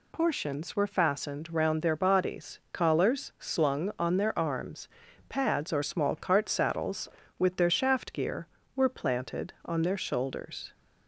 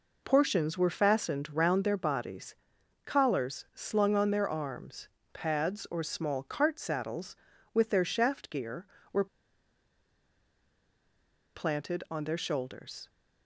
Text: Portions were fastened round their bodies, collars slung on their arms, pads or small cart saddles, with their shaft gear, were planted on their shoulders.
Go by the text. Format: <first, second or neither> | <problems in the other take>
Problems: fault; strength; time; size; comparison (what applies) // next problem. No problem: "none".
first | pauses between "were" and "planted"; strong; at 9.2 s; 2.3 s long